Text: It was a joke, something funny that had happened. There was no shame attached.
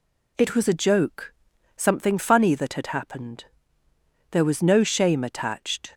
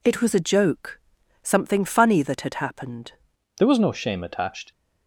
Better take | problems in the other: first | changes voice at "There"; from 3.5 s on; 1.2 s long

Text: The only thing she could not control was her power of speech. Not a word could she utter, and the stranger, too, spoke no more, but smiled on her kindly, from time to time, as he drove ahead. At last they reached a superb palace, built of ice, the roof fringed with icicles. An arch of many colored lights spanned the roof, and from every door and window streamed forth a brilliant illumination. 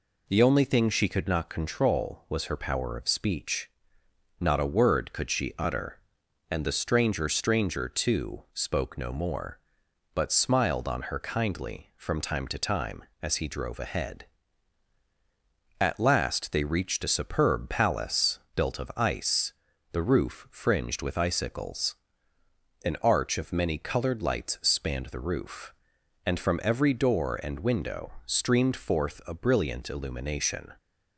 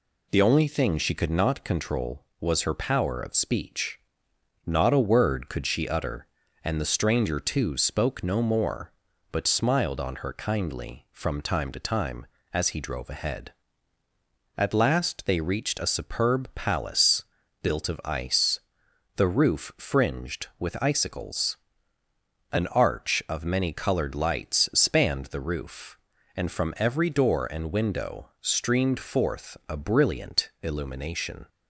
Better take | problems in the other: second | says "stranger" twice; at 7.2 s

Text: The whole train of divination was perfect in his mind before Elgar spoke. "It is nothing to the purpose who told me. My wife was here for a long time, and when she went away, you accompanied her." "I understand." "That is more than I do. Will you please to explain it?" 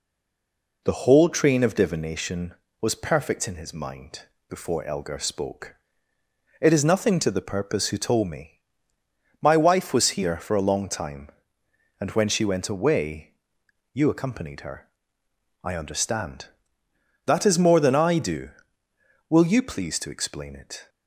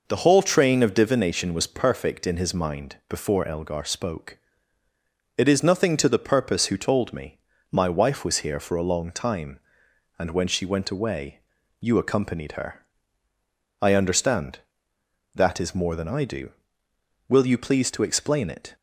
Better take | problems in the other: second | stays silent before the first word; slight; until 0.8 s; 0.8 s long // pauses between "mind" and "before"; slight; at 4.2 s; 0.26 s long

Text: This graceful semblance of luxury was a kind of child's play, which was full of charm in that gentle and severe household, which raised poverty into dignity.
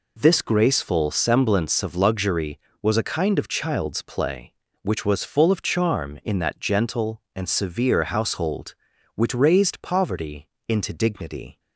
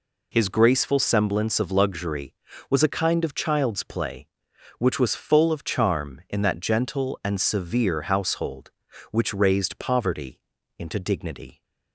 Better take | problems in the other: first | says "His" for "This"; at 0.3 s // pauses between "poverty" and "into"; at 10.4 s; 0.38 s long; slight in the first

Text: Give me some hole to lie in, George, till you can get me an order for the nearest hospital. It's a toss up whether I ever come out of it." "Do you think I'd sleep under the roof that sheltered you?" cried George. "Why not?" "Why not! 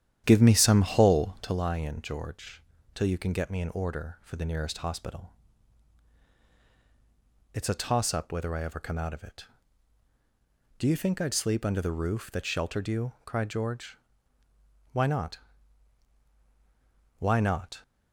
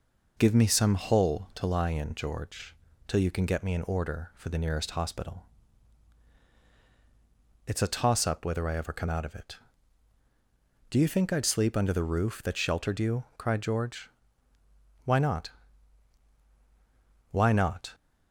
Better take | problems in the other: second | starts louder than the rest; strong; until 1.6 s; 10.5 dB

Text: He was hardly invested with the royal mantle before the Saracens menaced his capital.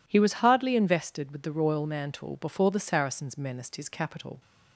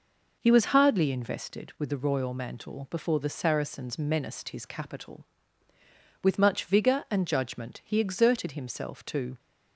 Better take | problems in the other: first | goes on to say "With much vigour and judgment he exerted himself to"; strong; from 6.2 s on; 3.1 s long

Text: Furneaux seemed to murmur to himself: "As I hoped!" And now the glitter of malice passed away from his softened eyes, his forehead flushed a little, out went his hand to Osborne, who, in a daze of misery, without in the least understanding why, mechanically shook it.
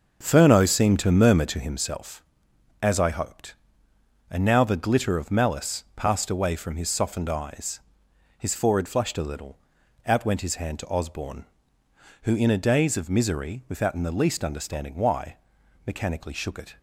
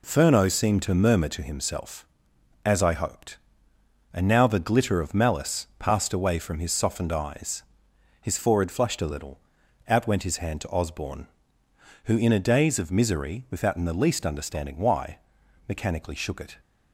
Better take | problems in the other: second | starts louder than the rest; noticeable; until 1.9 s; 6 dB

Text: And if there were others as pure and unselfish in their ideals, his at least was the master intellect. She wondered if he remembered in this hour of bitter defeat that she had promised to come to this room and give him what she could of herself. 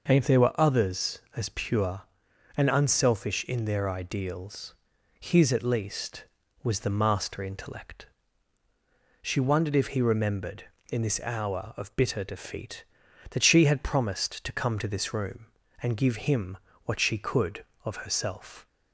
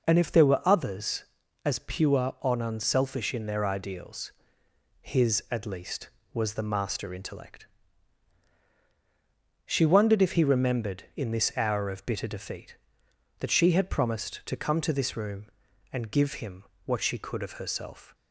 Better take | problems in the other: neither | pauses between "him" and "what"; slight; the same in both

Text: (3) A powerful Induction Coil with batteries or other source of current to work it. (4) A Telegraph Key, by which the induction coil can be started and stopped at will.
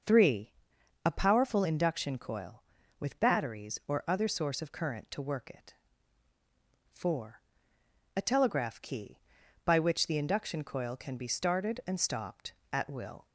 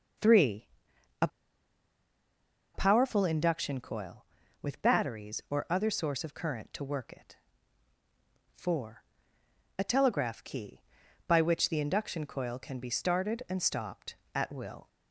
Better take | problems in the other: first | starts louder than the rest; until 3.2 s; 6 dB; also in the first // pauses between "A" and "powerful"; strong; at 1.2 s; 1.4 s long

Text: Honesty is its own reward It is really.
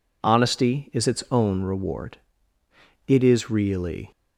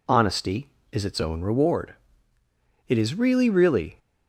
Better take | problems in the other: first | pauses between "reward" and "It"; noticeable; at 1.9 s; 0.94 s long; noticeable in the first // says "really" twice; at 3.4 s

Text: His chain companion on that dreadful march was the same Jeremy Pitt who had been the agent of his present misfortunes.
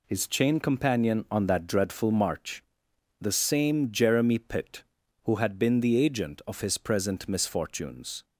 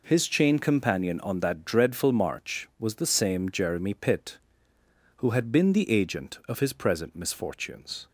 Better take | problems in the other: second | skips "was"; at 2.9 s

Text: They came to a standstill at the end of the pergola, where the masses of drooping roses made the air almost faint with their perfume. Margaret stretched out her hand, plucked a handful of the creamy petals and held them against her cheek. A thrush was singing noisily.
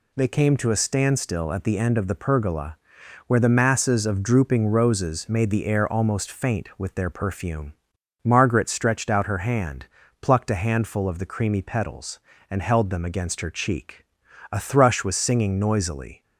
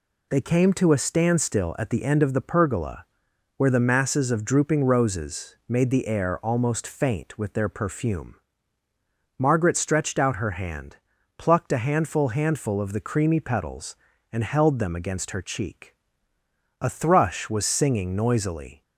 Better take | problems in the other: first | says "handful" twice; at 12.2 s

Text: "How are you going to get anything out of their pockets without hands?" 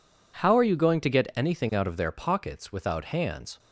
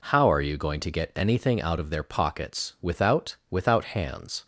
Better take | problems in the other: first | says "without" twice; at 3.4 s

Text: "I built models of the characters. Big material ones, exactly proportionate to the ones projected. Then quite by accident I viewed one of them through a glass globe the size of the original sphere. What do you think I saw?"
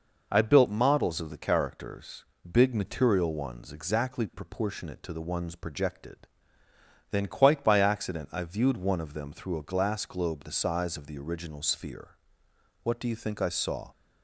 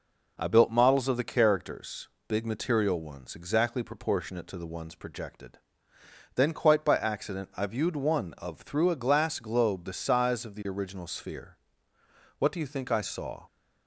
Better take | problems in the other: first | skips "them"; at 8.6 s

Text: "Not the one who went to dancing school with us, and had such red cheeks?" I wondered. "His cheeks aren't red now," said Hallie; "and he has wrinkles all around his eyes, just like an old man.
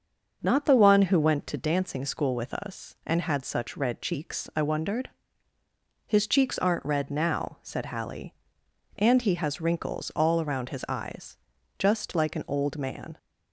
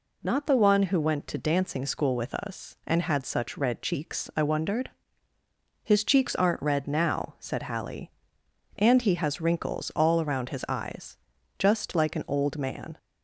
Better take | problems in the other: second | starts louder than the rest; until 1.7 s; 6 dB

